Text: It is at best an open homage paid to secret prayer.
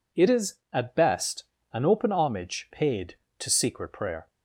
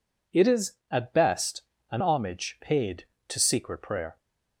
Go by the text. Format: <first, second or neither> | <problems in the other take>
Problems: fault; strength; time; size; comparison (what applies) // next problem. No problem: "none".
first | pauses between "best" and "an"; slight; at 1.6 s; 0.28 s long; slight in the first // skips "open"; at 2.0 s